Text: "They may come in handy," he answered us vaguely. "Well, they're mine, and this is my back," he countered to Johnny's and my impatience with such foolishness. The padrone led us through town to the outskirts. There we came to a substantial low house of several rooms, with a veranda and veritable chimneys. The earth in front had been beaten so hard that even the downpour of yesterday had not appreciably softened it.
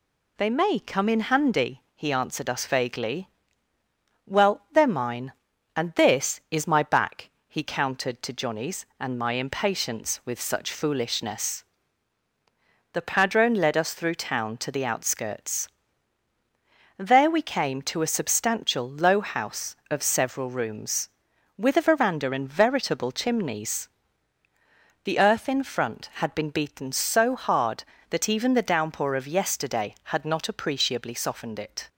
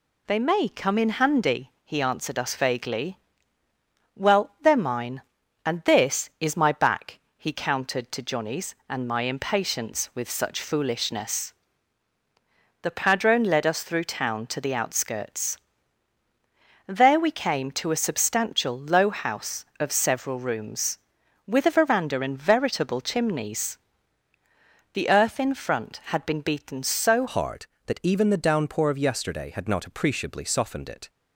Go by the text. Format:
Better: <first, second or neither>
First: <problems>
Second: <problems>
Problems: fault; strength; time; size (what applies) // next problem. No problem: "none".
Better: first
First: none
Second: changes voice at "hard"; from 27.2 s on; 3.8 s long